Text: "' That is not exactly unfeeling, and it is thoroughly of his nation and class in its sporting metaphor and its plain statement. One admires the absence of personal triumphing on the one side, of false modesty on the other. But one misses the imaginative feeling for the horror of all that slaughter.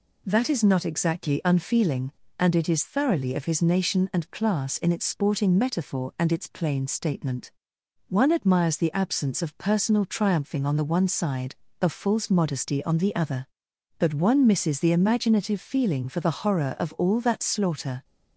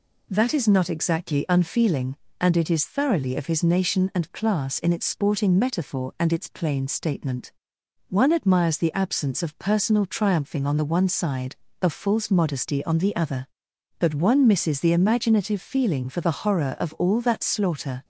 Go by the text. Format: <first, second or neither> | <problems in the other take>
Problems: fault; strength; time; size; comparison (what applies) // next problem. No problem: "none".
neither | none